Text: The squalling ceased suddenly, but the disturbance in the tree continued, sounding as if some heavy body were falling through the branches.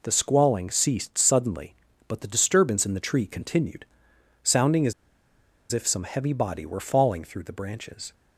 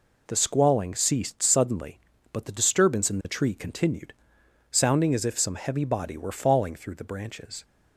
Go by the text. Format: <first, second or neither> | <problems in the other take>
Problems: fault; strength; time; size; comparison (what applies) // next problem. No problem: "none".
second | pauses between "as" and "if"; noticeable; at 4.9 s; 0.79 s long